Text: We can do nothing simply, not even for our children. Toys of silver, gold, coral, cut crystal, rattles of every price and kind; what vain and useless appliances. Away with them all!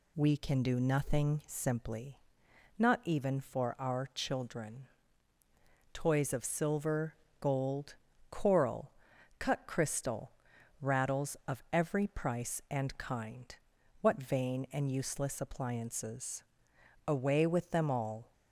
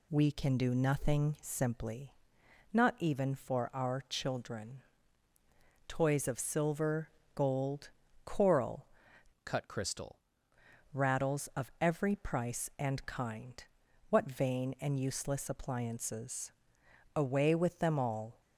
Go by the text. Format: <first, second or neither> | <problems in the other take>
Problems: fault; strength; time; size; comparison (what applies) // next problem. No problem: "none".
first | changes voice from "cut" to "crystal"; from 9.4 to 10.2 s; 0.8 s long